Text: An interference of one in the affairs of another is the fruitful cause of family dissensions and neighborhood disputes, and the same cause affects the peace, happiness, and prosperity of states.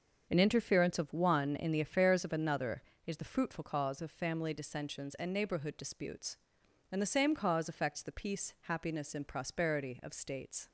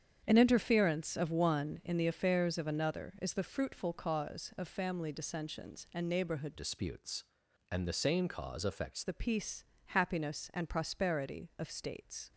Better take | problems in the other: first | starts louder than the rest; strong; until 1.2 s; 8 dB; also in the first // changes voice from "disputes" to "affects"; from 6.5 to 9.0 s; 2.5 s long

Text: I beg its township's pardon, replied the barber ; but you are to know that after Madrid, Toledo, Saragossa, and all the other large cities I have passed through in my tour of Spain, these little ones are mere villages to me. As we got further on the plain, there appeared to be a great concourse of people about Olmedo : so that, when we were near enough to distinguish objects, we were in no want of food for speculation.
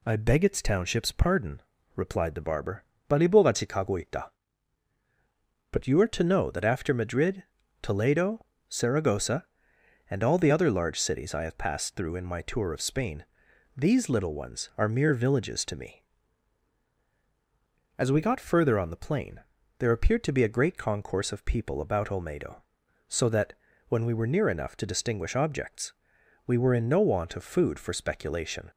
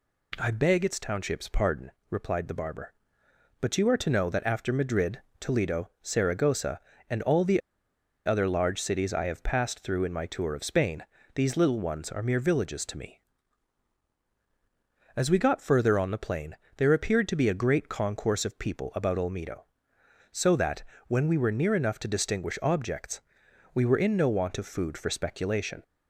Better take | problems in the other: first | pauses between "the" and "other"; noticeable; at 7.6 s; 0.66 s long

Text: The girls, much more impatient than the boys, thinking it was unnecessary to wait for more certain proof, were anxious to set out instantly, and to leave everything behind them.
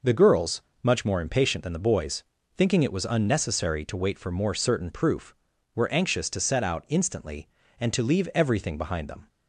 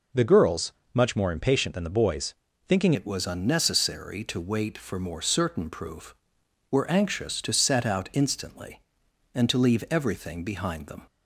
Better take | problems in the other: first | changes voice at "it"; from 2.9 s on; 8.1 s long

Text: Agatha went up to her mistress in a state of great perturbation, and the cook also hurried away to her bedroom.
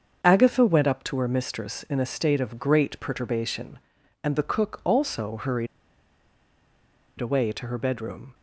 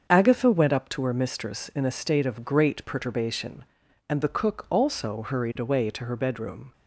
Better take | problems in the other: second | starts louder than the rest; until 1.2 s; 7 dB; also in the second // pauses between "hurried" and "away"; strong; at 5.6 s; 1.5 s long

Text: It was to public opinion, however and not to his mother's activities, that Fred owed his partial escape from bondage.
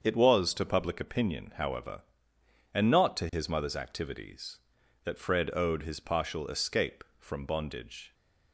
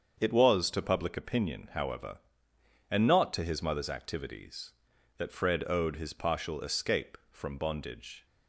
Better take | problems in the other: neither | starts louder than the rest; the same in both

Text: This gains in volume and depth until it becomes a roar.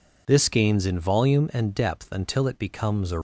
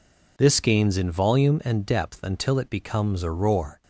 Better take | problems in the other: second | stops before "roar"; at 3.1 s

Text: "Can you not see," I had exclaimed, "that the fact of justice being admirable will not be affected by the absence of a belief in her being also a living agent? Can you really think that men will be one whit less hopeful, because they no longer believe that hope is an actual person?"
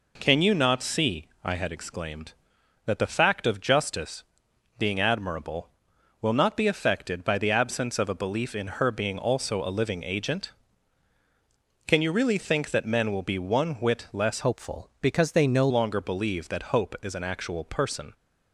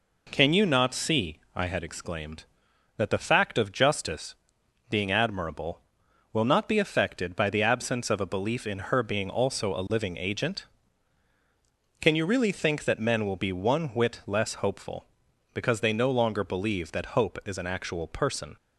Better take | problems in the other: second | pauses between "justice" and "being"; noticeable; at 4.2 s; 0.54 s long; noticeable in the second // changes voice from "hopeful" to "no"; from 14.4 to 15.6 s; 1.2 s long

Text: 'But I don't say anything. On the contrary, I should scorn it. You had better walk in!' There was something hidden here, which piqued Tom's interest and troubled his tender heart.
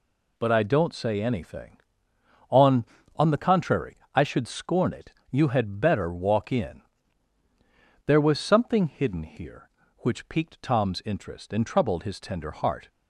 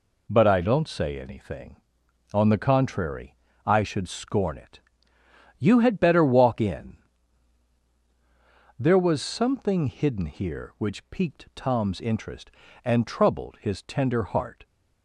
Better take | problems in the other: second | says "On" twice; at 3.1 s

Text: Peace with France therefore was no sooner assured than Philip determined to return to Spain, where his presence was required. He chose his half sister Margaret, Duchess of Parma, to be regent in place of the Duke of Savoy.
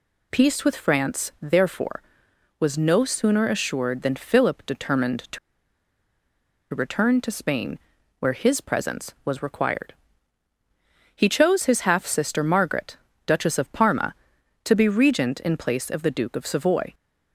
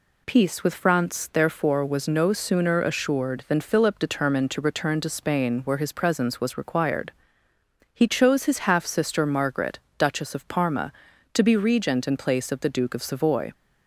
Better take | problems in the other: second | pauses between "to" and "return"; strong; at 5.3 s; 1.3 s long

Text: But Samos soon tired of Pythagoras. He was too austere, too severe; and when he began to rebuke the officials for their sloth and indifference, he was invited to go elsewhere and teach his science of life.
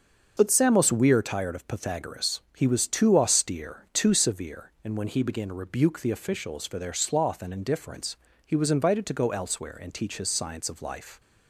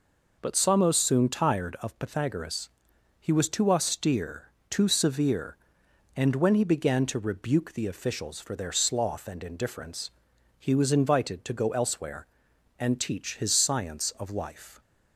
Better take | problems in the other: second | starts louder than the rest; until 1.3 s; 6.5 dB // says "weir" for "soon"; at 0.9 s

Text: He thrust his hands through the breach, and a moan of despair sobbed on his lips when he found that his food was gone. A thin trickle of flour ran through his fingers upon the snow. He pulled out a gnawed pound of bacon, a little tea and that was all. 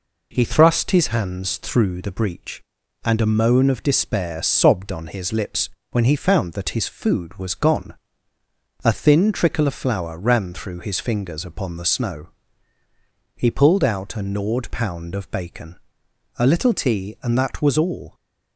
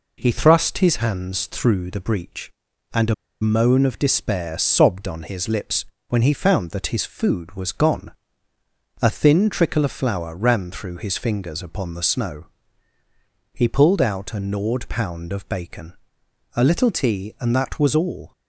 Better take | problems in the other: first | pauses between "a" and "moan"; slight; at 3.1 s; 0.27 s long // pauses between "lips" and "when"; slight; at 5.8 s; 0.24 s long; slight in the first

